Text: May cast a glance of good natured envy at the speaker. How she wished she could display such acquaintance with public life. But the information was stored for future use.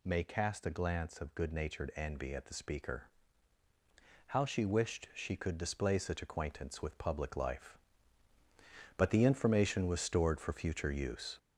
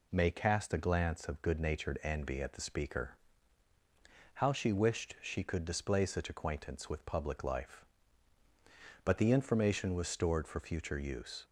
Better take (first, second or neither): second